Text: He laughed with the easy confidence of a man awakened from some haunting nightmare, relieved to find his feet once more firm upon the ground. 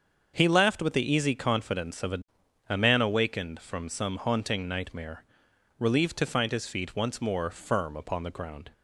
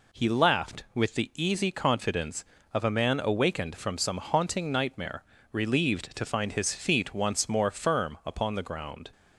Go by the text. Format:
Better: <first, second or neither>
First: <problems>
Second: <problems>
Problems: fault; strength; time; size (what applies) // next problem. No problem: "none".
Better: second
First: starts louder than the rest; until 1.3 s; 7 dB // says "a" twice; at 2.6 s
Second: none